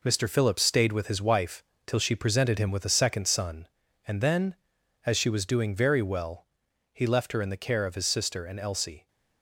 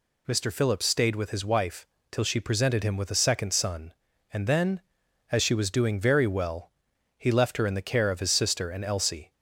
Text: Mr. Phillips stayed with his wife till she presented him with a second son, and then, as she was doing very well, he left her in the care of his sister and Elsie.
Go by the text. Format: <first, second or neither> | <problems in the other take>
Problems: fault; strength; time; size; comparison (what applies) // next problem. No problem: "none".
second | gets quieter; throughout; 6.5 dB // pauses between "wife" and "till"; slight; at 1.6 s; 0.22 s long; slight in the second